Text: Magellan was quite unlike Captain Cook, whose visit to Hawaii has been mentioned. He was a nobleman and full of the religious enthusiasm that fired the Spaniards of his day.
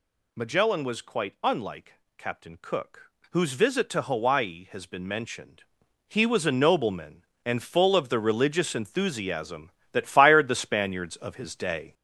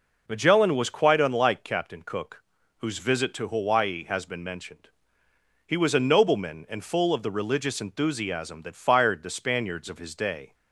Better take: second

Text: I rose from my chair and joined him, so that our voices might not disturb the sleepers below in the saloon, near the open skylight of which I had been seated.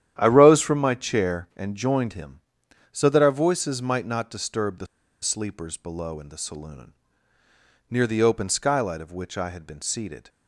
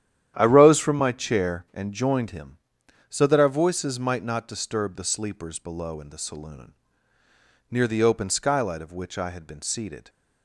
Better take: second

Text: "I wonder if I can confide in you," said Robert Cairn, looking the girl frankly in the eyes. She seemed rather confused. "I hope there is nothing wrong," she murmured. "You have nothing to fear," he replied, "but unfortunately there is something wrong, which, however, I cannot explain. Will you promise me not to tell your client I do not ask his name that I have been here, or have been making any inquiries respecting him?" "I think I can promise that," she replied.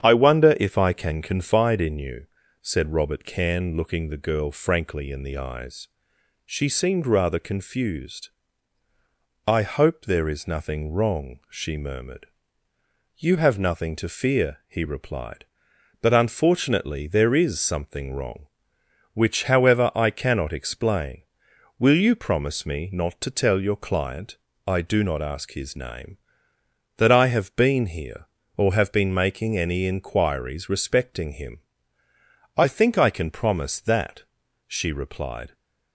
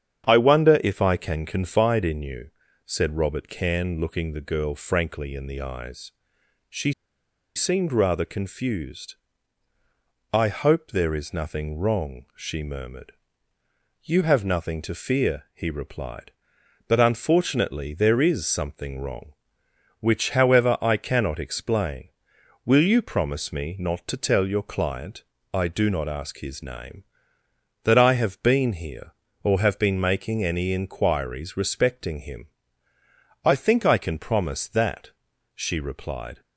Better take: first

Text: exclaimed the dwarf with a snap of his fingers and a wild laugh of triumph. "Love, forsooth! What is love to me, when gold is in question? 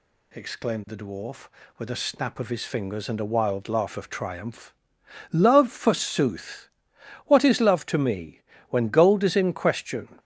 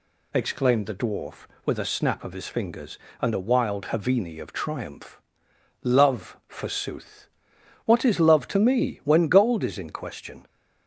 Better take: first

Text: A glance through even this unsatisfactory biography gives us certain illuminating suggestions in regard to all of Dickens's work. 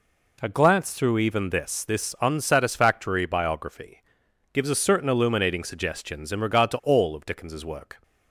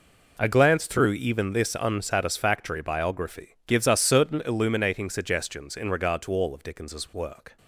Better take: second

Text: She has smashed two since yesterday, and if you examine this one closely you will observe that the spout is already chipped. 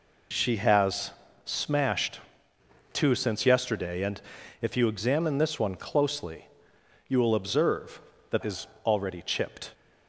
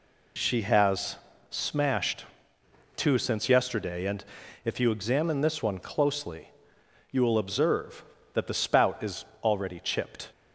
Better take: second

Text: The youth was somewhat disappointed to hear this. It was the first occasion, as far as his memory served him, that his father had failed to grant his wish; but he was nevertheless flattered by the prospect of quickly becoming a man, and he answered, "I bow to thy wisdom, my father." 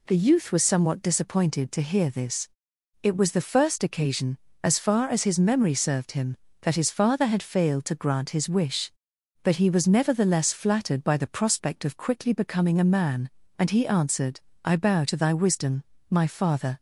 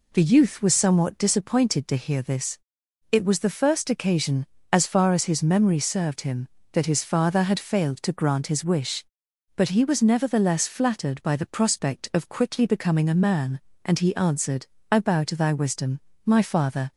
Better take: neither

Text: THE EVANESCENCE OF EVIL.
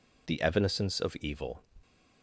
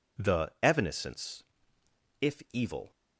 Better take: first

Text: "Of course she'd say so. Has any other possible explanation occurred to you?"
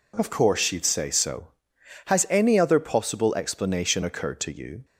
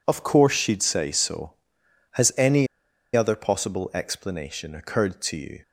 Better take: first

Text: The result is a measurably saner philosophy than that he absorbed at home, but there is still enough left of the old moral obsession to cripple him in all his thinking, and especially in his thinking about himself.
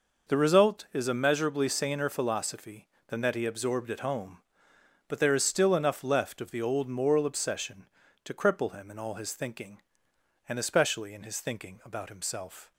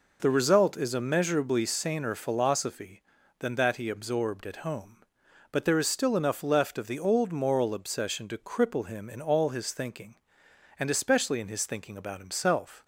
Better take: neither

